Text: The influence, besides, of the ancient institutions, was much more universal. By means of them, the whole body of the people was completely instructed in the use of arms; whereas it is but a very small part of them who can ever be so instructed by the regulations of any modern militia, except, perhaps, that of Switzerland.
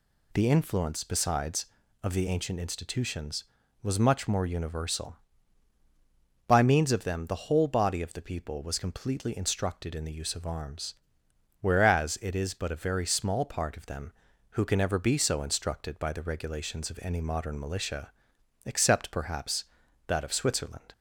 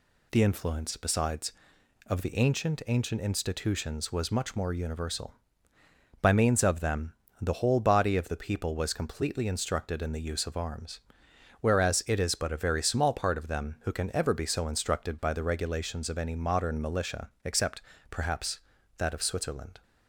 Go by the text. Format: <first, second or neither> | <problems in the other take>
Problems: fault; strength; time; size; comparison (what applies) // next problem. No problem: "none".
first | says "ancient" twice; at 2.8 s